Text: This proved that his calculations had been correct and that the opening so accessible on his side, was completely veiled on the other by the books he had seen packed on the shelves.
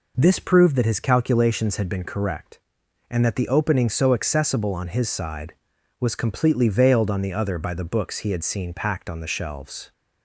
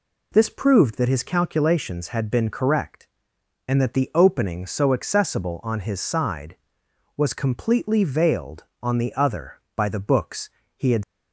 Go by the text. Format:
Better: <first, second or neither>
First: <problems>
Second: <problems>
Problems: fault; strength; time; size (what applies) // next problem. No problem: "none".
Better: first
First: none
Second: pauses between "books" and "he"; slight; at 10.4 s; 0.26 s long // stops before "seen packed on the shelves"; at 11.0 s